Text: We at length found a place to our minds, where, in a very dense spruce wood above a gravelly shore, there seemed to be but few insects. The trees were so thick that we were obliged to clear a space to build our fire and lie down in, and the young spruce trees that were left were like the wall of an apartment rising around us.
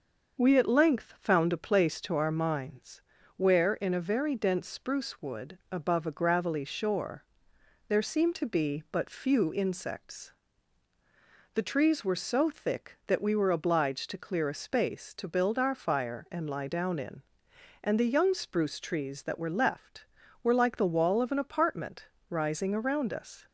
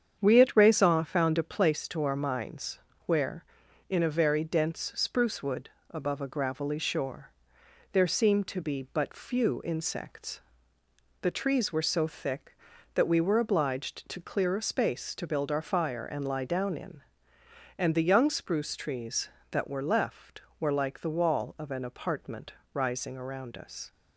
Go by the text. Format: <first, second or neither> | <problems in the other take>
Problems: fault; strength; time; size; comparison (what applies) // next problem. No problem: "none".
first | starts louder than the rest; strong; until 1.2 s; 8 dB; also in the first // says "raison" for "length"; at 0.5 s // pauses between "wood" and "above"; slight; at 5.6 s; 0.22 s long // pauses between "apartment" and "rising"; slight; at 22.5 s; 0.20 s long; slight in the first